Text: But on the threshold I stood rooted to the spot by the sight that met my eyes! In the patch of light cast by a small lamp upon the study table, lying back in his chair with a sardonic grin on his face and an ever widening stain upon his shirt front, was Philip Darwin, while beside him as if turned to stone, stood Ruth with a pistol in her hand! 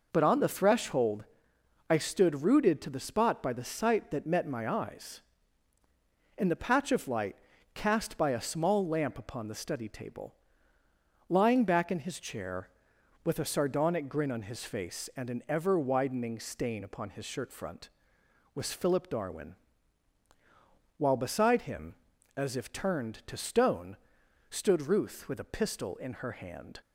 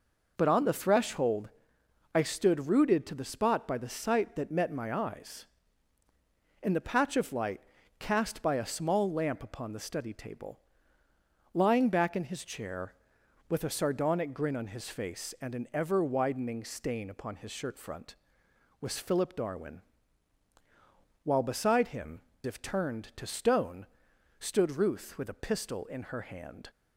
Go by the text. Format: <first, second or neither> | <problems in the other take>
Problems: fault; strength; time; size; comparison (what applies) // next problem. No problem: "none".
first | pauses between "threshold" and "I"; noticeable; at 1.4 s; 0.66 s long; noticeable in the first // pauses between "light" and "cast"; at 7.6 s; 0.38 s long; also in the first // skips "as"; at 22.3 s